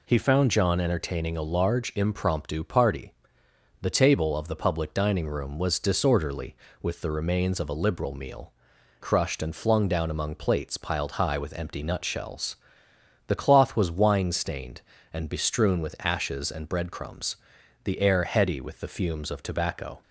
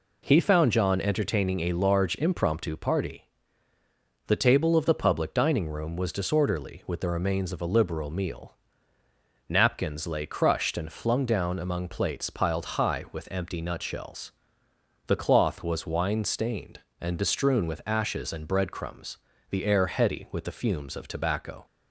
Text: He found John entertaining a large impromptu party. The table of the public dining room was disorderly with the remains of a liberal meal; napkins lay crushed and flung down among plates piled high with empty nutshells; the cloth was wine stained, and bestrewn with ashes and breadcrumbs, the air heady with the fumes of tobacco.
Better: second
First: skips "napkins lay"; at 8.7 s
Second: none

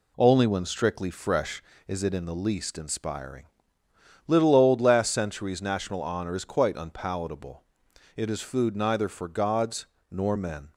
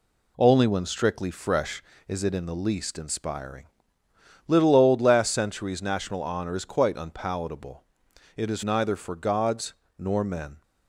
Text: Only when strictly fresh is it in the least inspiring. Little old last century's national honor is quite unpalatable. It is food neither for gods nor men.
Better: first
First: pauses between "gods" and "nor"; slight; at 9.8 s; 0.24 s long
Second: skips "food"; at 8.6 s // pauses between "gods" and "nor"; slight; at 9.7 s; 0.24 s long

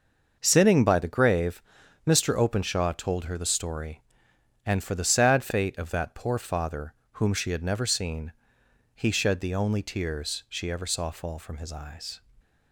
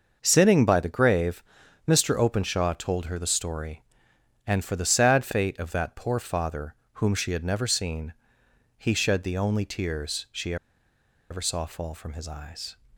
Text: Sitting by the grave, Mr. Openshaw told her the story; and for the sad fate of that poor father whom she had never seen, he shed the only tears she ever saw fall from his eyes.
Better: first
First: starts louder than the rest; noticeable; until 1.4 s; 6 dB // pauses between "father" and "whom"; slight; at 6.9 s; 0.20 s long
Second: starts louder than the rest; noticeable; until 1.2 s; 6 dB // pauses between "father" and "whom"; slight; at 6.7 s; 0.20 s long // pauses between "she" and "ever"; noticeable; at 10.5 s; 0.75 s long

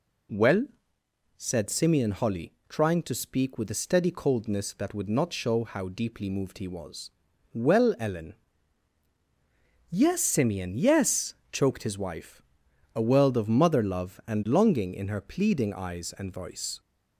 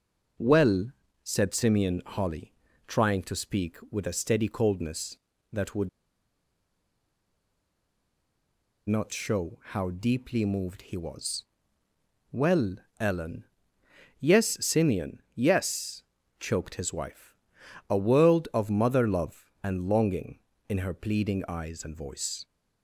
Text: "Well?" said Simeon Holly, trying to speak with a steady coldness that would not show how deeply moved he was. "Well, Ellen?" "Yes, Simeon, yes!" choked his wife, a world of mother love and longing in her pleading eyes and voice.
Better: first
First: none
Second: pauses between "would" and "not"; strong; at 5.8 s; 2.9 s long

